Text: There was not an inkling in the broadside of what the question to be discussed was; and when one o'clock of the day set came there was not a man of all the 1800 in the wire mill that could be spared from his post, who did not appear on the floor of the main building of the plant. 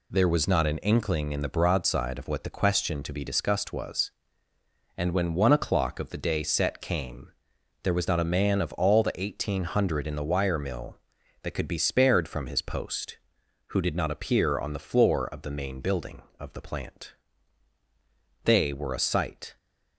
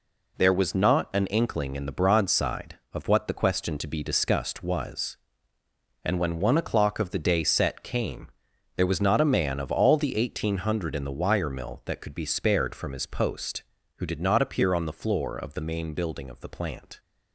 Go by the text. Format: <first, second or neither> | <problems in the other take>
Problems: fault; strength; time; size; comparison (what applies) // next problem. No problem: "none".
second | pauses between "came" and "there"; noticeable; at 7.2 s; 0.54 s long; noticeable in the second // goes on to say "They were a sight"; noticeable; from 18.4 s on; 1.1 s long